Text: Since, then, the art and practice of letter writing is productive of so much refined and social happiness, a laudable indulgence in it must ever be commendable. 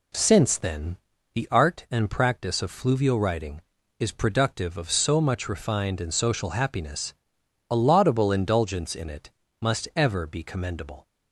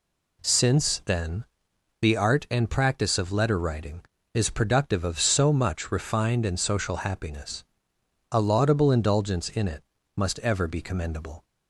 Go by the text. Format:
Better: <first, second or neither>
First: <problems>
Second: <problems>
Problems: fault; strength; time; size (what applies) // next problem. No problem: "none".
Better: second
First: says "fluvial" for "letter"; at 2.6 s // pauses between "it" and "must"; slight; at 9.3 s; 0.28 s long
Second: pauses between "it" and "must"; slight; at 9.8 s; 0.34 s long